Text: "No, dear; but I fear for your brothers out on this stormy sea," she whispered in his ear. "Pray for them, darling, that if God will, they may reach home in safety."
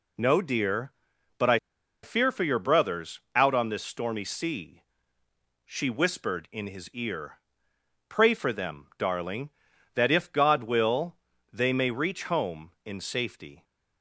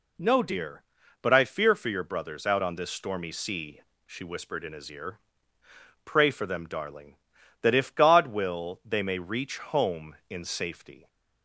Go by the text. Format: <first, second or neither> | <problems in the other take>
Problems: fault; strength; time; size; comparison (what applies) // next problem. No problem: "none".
second | pauses between "I" and "fear"; at 1.5 s; 0.45 s long